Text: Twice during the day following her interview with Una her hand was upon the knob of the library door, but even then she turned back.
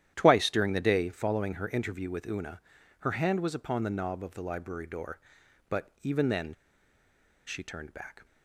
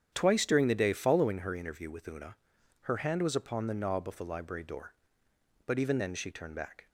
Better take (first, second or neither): second